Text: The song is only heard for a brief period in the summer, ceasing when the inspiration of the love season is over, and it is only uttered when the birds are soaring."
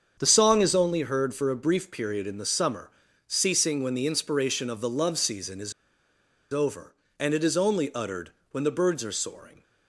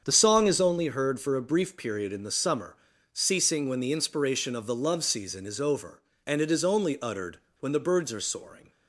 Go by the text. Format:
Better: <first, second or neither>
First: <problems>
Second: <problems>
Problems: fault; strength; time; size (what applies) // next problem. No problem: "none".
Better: second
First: starts louder than the rest; until 1.2 s; 7 dB // pauses between "is" and "over"; noticeable; at 5.7 s; 0.81 s long // pauses between "uttered" and "when"; slight; at 8.3 s; 0.22 s long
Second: starts louder than the rest; strong; until 1.0 s; 7 dB // pauses between "uttered" and "when"; slight; at 7.3 s; 0.23 s long